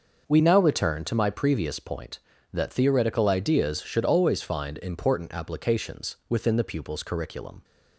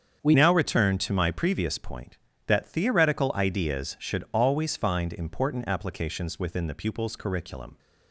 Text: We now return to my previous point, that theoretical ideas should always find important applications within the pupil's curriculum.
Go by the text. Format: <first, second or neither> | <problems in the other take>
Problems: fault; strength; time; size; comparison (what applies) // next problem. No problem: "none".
first | starts louder than the rest; strong; until 1.2 s; 7.5 dB; also in the first // changes voice at "now"; from 0.3 s on; 7.4 s long